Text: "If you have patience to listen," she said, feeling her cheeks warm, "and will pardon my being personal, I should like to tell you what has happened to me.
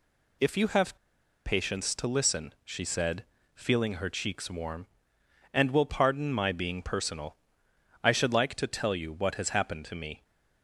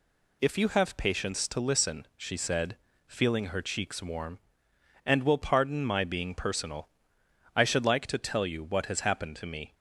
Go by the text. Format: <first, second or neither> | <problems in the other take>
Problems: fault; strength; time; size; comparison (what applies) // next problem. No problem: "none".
second | pauses between "have" and "patience"; noticeable; at 0.9 s; 0.49 s long